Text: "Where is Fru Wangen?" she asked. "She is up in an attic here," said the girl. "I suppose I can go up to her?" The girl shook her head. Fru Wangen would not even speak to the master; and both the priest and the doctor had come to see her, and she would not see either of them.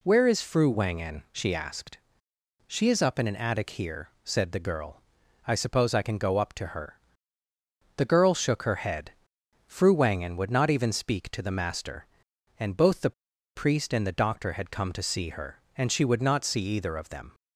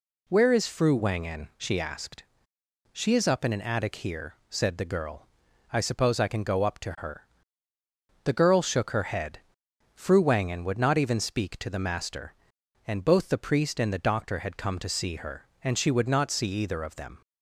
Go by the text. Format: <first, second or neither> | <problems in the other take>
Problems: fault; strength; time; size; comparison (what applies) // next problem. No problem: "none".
second | pauses between "the" and "priest"; at 13.1 s; 0.44 s long